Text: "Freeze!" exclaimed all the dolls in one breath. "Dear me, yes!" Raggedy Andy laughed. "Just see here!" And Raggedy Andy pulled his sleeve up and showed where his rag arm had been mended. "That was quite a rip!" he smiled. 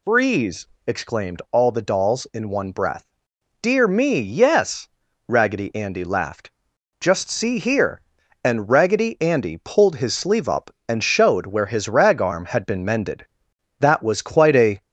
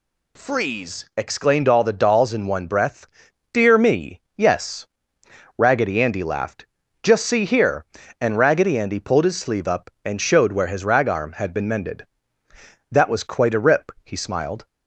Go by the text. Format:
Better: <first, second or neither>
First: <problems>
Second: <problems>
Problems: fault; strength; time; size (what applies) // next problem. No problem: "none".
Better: second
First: stops before "rip he smiled"; at 14.8 s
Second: none